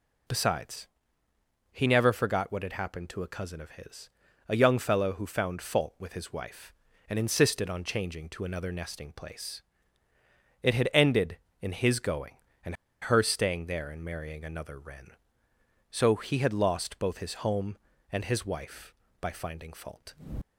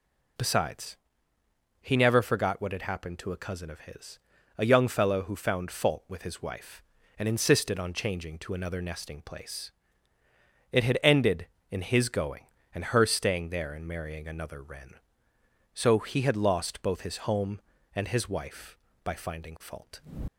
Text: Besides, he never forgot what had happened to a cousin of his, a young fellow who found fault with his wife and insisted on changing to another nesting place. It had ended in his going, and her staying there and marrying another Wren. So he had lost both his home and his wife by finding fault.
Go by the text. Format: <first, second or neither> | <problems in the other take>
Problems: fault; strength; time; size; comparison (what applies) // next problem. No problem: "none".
second | pauses between "and" and "her"; slight; at 12.7 s; 0.27 s long